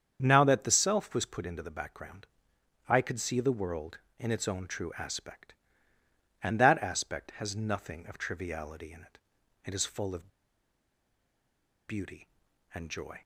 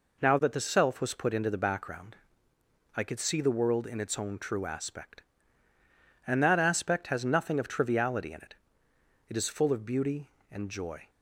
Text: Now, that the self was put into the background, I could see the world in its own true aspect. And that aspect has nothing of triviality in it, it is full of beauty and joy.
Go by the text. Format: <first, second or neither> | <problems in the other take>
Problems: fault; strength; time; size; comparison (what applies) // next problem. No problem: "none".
second | starts louder than the rest; strong; until 1.2 s; 7.5 dB // pauses between "of" and "beauty"; strong; at 10.2 s; 1.5 s long